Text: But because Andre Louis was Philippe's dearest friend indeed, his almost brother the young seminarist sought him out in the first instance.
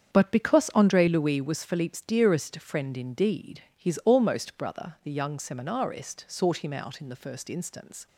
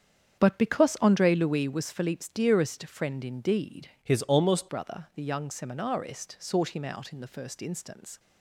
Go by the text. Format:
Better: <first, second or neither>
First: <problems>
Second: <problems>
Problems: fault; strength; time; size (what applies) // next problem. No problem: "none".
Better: first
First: starts louder than the rest; strong; until 1.1 s; 8 dB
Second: starts louder than the rest; strong; until 1.4 s; 8 dB // changes voice from "his" to "almost"; from 4.0 to 4.6 s; 0.6 s long